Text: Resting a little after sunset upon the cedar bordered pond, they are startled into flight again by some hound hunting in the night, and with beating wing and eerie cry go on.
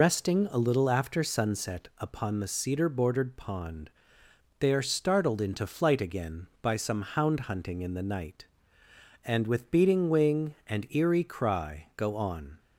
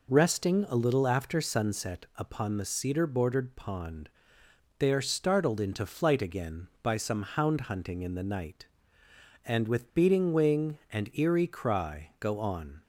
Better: second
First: loses the start of "Resting"; at 0.0 s; 95 ms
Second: none

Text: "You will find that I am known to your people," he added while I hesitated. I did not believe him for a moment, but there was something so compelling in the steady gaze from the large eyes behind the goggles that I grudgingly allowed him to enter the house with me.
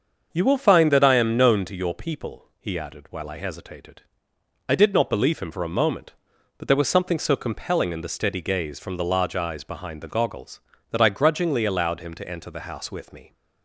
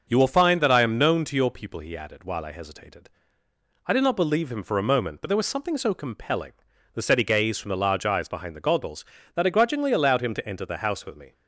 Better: first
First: starts louder than the rest; until 1.3 s; 6.5 dB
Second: starts louder than the rest; noticeable; until 1.1 s; 6 dB // skips "in"; at 6.7 s

